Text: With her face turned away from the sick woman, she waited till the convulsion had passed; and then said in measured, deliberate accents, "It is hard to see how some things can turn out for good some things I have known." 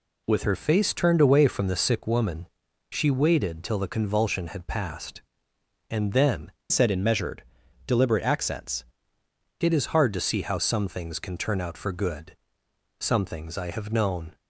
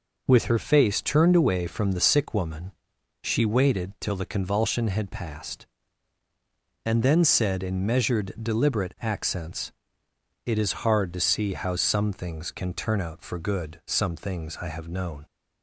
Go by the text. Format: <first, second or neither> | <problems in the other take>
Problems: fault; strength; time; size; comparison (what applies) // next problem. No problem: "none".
second | changes voice from "said" to "accents"; from 6.6 to 8.8 s; 2.2 s long // pauses between "good" and "some"; noticeable; at 12.3 s; 0.62 s long